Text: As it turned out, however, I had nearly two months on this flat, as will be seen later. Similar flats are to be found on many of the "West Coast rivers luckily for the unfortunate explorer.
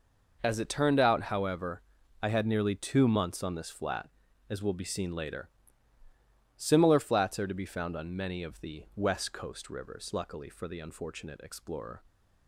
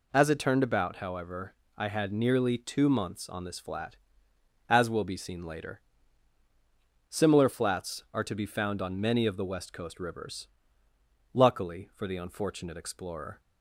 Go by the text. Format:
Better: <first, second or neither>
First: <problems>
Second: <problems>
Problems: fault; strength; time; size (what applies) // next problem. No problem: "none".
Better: first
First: none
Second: says "about" for "out"; at 0.6 s // pauses between "rivers" and "luckily"; noticeable; at 10.4 s; 0.84 s long